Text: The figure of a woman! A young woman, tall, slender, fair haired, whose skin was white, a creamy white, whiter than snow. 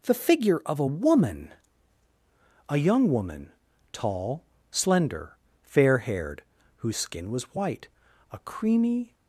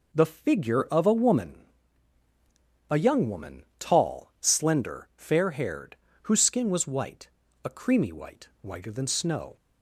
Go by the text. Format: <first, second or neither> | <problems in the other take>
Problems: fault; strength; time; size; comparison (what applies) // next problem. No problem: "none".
second | stops before "white whiter than snow"; at 9.1 s